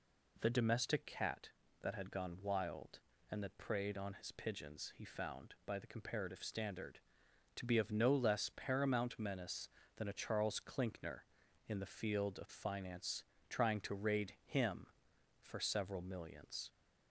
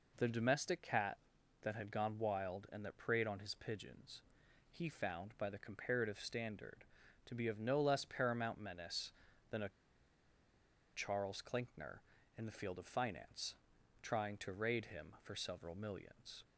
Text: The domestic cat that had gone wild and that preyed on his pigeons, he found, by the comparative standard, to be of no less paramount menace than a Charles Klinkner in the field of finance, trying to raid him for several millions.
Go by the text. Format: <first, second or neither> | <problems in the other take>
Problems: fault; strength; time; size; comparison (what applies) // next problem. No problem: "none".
first | pauses between "a" and "Charles"; strong; at 9.6 s; 1.2 s long